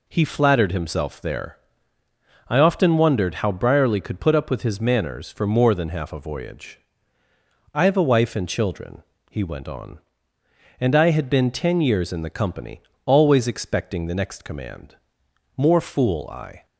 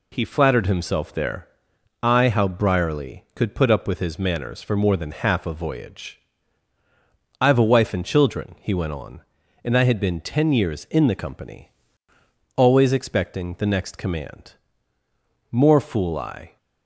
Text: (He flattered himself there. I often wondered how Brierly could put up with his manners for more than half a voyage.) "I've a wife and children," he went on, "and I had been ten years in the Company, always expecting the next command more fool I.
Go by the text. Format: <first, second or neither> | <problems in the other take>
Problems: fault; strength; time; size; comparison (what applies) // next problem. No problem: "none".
first | skips "often wondered"; at 2.2 s // pauses between "command" and "more"; noticeable; at 14.5 s; 0.98 s long; noticeable in the first